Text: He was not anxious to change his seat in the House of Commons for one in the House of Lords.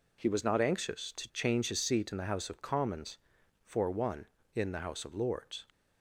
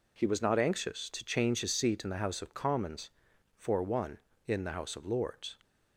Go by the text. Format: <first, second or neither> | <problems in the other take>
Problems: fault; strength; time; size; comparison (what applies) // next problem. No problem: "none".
neither | none